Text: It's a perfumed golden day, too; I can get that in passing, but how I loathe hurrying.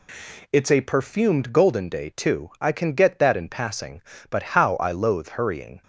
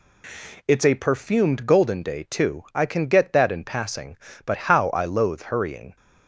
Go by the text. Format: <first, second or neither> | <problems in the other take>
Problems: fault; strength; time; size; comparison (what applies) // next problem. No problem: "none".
neither | none